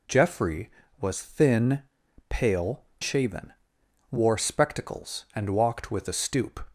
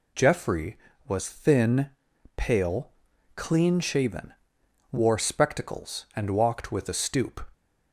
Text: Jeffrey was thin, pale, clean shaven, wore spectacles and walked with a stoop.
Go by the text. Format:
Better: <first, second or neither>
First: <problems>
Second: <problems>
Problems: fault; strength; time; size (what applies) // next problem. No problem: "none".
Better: second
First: skips "clean"; at 2.9 s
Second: none